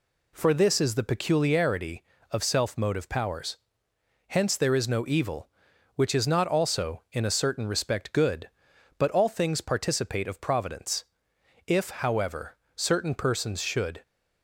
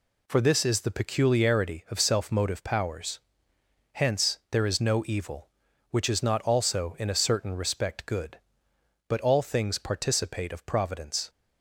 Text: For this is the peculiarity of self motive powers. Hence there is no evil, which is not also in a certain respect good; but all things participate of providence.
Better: second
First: goes on to say "If however certain persons should"; strong; from 11.6 s on; 2.3 s long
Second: none

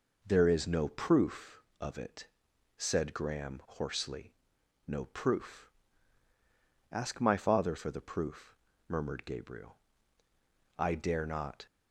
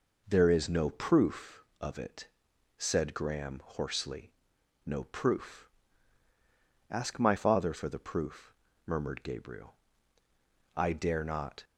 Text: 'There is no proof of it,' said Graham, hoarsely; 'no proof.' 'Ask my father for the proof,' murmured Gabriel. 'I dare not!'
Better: neither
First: none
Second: none

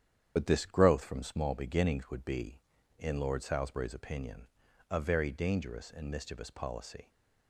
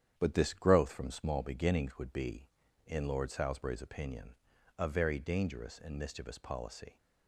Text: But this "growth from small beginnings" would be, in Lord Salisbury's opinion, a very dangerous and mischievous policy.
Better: second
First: loses the start of "But"; at 0.3 s; 55 ms // starts louder than the rest; strong; until 1.3 s; 9 dB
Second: starts louder than the rest; strong; until 1.1 s; 9 dB

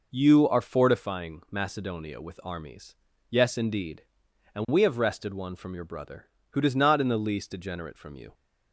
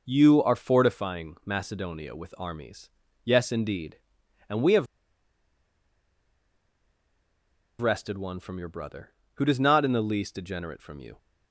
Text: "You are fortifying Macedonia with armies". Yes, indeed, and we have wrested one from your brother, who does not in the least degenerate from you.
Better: first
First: none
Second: pauses between "have" and "wrested"; strong; at 4.8 s; 2.9 s long

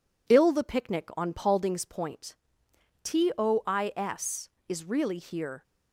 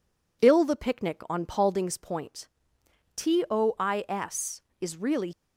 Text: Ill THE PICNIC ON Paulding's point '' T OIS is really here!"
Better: first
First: none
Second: stops before "here"; at 5.3 s

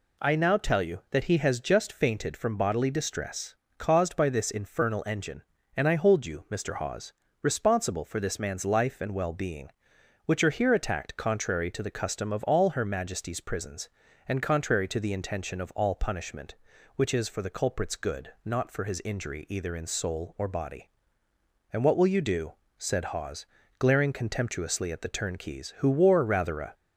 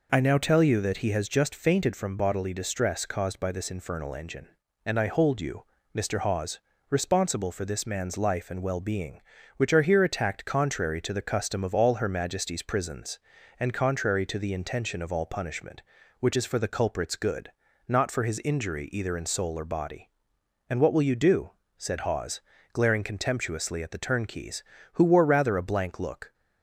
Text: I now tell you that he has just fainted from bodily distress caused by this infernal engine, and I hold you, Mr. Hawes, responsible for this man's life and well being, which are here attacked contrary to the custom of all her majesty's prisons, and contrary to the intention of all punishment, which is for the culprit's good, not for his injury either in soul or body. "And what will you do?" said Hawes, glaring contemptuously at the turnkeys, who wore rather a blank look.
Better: second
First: pauses between "distress" and "caused"; slight; at 3.5 s; 0.24 s long // stops before "blank look"; at 26.7 s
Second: none

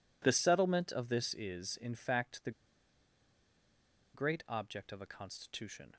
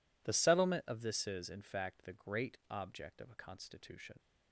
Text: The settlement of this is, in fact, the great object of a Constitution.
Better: second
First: pauses between "the" and "great"; strong; at 2.5 s; 1.6 s long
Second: none

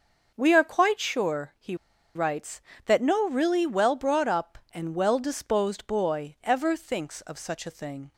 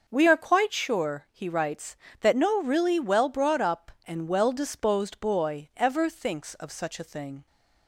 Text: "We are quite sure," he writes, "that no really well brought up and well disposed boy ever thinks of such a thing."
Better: second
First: starts louder than the rest; noticeable; until 1.3 s; 6 dB // pauses between "he" and "writes"; at 1.7 s; 0.40 s long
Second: none

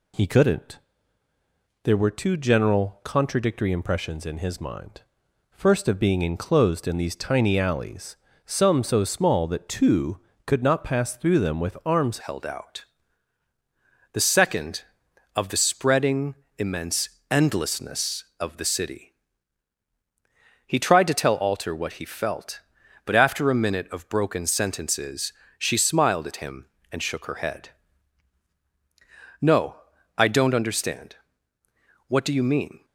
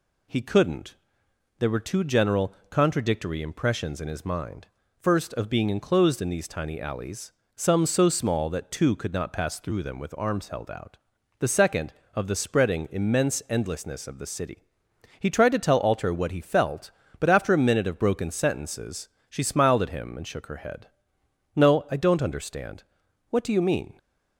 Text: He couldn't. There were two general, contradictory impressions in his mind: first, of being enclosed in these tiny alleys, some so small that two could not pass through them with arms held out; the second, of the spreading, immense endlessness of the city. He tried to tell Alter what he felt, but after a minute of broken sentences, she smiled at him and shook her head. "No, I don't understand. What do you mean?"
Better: second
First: changes voice at "held"; from 12.2 s on; 20.6 s long // pauses between "immense" and "endlessness"; slight; at 17.0 s; 0.22 s long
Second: none

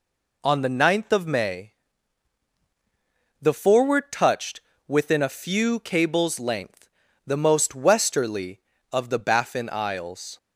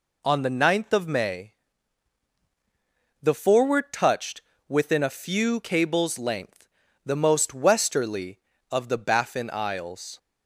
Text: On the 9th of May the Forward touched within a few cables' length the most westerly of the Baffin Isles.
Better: neither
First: pauses between "May" and "the"; strong; at 1.7 s; 1.6 s long // pauses between "touched" and "within"; slight; at 4.6 s; 0.26 s long // pauses between "length" and "the"; at 6.8 s; 0.40 s long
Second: pauses between "May" and "the"; strong; at 1.5 s; 1.6 s long // pauses between "touched" and "within"; slight; at 4.4 s; 0.26 s long // pauses between "length" and "the"; at 6.6 s; 0.40 s long

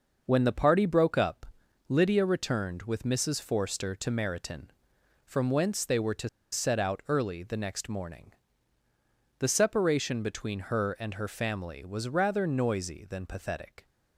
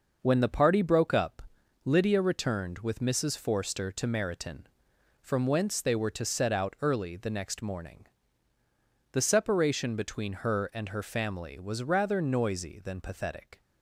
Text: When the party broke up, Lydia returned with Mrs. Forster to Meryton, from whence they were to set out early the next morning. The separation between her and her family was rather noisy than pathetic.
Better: second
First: pauses between "to" and "set"; slight; at 6.2 s; 0.23 s long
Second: none

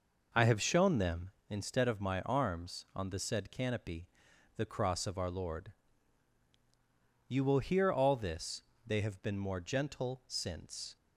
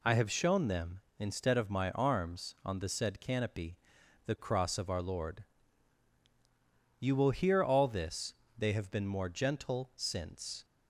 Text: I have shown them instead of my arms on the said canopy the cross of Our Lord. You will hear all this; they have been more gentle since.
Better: second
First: starts louder than the rest; noticeable; until 1.5 s; 5.5 dB // pauses between "canopy" and "the"; noticeable; at 4.0 s; 0.50 s long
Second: pauses between "canopy" and "the"; noticeable; at 3.7 s; 0.50 s long

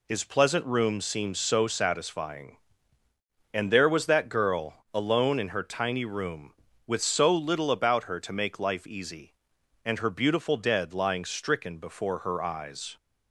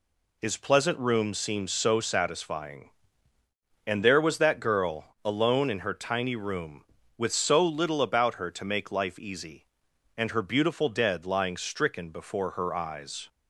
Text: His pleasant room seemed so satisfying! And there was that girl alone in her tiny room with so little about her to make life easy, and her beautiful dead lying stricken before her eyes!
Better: neither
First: none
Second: none

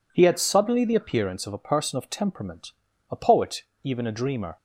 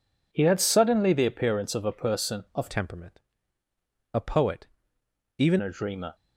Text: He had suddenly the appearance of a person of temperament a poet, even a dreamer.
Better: first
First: pauses between "temperament" and "a"; at 2.7 s; 0.38 s long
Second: changes voice from "temperament" to "even"; from 2.7 to 5.5 s; 2.8 s long // pauses between "temperament" and "a"; noticeable; at 3.1 s; 0.94 s long

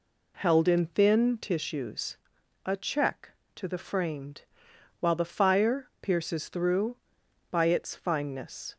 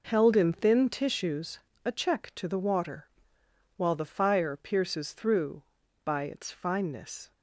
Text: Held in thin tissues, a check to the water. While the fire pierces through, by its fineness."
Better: second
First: says "framed" for "water"; at 3.7 s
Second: none

